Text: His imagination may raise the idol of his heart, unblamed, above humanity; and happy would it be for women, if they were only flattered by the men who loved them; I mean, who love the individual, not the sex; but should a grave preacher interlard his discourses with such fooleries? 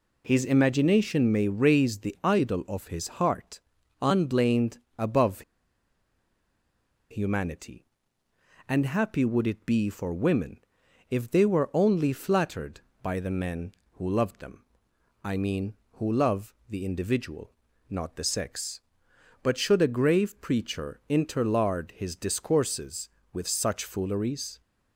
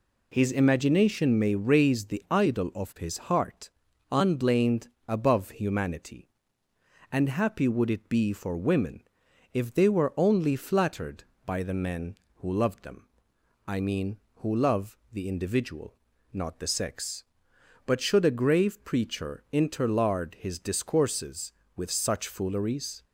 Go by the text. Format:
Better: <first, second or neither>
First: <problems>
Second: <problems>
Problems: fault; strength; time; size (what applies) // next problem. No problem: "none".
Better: second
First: pauses between "above" and "humanity"; strong; at 5.4 s; 1.6 s long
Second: none